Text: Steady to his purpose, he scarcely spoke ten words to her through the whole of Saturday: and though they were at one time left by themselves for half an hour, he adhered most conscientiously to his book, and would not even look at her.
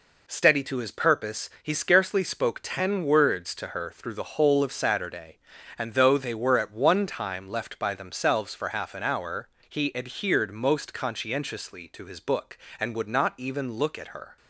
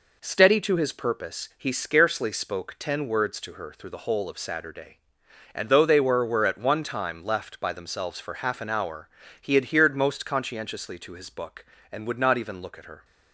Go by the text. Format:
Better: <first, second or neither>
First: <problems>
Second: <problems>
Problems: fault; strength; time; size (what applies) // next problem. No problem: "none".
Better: first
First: none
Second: says "were" twice; at 6.2 s